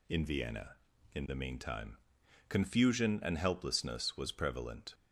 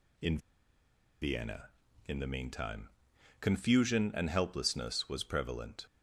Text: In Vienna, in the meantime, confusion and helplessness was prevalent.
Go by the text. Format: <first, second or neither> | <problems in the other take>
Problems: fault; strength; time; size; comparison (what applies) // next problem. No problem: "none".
first | pauses between "In" and "Vienna"; noticeable; at 0.3 s; 0.83 s long